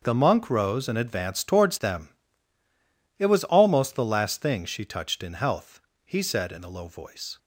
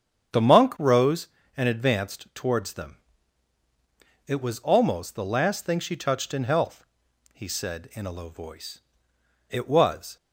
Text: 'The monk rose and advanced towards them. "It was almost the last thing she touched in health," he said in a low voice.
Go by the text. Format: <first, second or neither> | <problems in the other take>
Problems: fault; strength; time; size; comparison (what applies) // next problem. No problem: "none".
first | starts louder than the rest; strong; until 1.6 s; 8 dB; also in the first // goes on to say "It was"; noticeable; from 9.5 s on; 0.66 s long